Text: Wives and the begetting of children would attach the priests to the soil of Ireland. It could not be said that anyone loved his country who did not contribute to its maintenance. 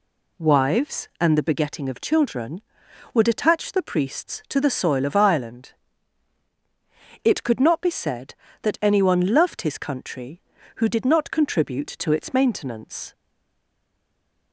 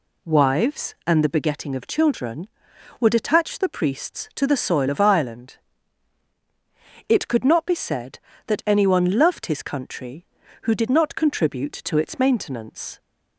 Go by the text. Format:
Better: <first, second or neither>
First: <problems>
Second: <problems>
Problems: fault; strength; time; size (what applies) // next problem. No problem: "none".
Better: second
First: stays silent after the last word; noticeable; from 13.1 s on; 1.4 s long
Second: none